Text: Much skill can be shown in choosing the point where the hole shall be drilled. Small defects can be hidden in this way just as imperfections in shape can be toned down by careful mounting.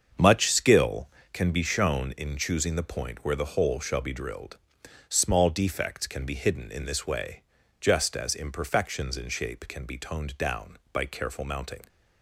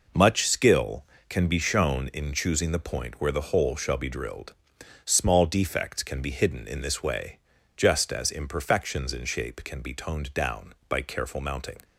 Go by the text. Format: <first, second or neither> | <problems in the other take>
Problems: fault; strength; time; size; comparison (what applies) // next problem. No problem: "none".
second | starts louder than the rest; until 1.5 s; 7 dB // pauses between "way" and "just"; at 7.3 s; 0.42 s long; also in the second